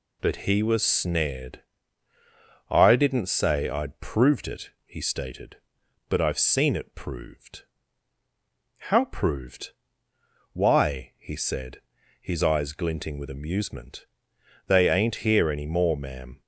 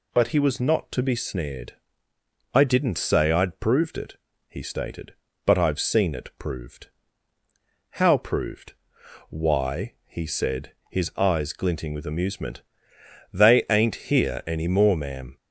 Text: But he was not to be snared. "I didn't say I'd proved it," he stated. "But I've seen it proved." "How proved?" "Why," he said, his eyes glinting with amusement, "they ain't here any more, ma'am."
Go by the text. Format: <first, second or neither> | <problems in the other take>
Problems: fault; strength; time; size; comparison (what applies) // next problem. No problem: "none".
second | skips "not to be"; at 0.8 s